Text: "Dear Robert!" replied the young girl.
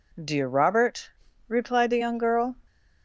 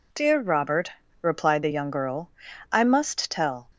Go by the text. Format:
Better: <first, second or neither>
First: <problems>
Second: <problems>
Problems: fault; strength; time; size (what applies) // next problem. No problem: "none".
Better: first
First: none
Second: goes on to say "I must tell"; noticeable; from 2.7 s on; 0.96 s long